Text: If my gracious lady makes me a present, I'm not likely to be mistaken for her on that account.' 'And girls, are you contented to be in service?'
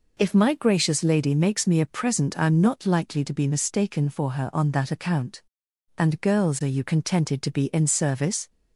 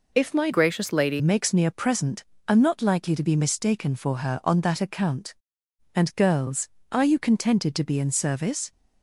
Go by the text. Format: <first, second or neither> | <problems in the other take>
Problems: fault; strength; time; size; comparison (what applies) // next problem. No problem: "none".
first | changes voice from "gracious" to "lady"; from 0.5 to 1.2 s; 0.7 s long